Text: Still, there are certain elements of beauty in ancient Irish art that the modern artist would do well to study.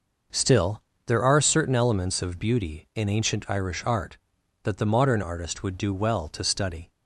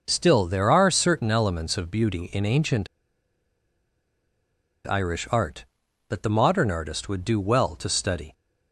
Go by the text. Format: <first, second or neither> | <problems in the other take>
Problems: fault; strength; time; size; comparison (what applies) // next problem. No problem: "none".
first | pauses between "ancient" and "Irish"; strong; at 2.8 s; 1.9 s long